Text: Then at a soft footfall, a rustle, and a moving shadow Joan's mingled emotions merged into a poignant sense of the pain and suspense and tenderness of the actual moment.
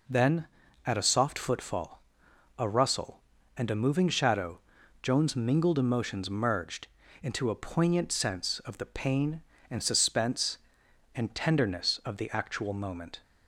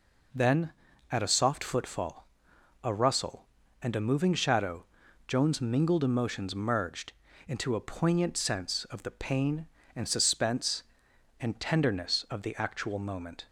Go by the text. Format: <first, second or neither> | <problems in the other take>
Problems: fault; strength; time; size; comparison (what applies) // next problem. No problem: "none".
neither | pauses between "shadow" and "Joan's"; the same in both // pauses between "merged" and "into"; slight; the same in both